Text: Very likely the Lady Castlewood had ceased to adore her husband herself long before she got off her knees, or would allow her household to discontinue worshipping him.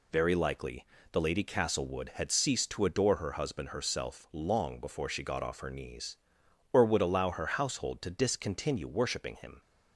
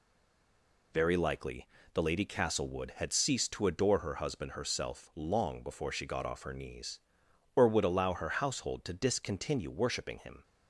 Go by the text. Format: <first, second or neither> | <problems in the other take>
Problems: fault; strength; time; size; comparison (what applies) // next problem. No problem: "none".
first | stays silent before the first word; slight; until 0.9 s; 0.9 s long // pauses between "likely" and "the"; slight; at 1.6 s; 0.24 s long; slight in the first